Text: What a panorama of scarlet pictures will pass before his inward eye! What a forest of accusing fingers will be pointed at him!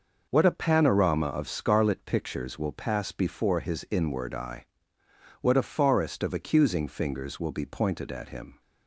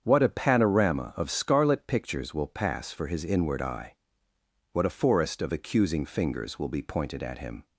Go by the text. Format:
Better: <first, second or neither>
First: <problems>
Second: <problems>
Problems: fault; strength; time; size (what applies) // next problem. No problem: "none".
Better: first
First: none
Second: starts louder than the rest; strong; until 1.0 s; 7.5 dB // says "for" for "before"; at 2.9 s